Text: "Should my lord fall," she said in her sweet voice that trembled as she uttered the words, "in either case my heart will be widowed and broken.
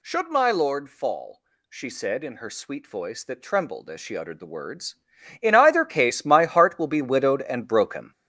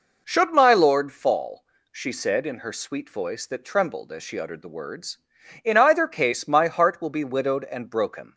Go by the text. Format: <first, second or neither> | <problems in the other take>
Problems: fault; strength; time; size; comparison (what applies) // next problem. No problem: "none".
second | gets louder; throughout; 7 dB